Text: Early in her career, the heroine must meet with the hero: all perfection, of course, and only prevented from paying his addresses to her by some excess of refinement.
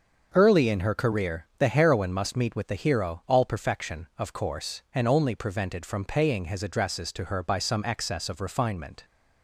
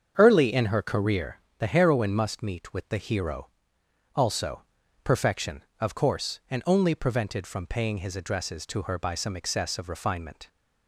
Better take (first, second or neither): first